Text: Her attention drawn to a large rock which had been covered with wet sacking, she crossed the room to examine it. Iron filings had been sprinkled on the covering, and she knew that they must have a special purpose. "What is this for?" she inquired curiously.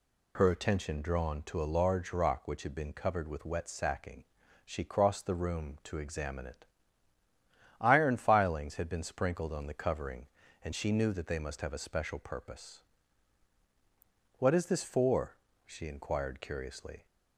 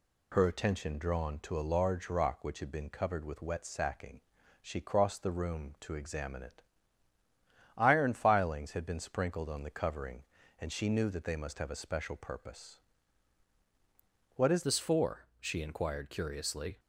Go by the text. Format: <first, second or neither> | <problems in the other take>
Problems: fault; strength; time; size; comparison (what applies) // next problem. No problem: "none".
first | changes voice at "this"; from 14.6 s on; 2.1 s long